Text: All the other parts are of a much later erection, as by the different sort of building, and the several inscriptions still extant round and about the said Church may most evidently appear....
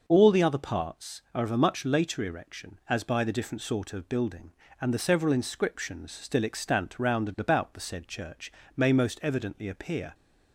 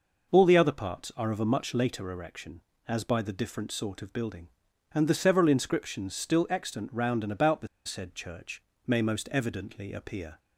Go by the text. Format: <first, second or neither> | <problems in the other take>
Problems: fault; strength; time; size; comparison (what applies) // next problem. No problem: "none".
first | pauses between "the" and "said"; slight; at 7.6 s; 0.18 s long // pauses between "Church" and "may"; slight; at 8.6 s; 0.24 s long; slight in the first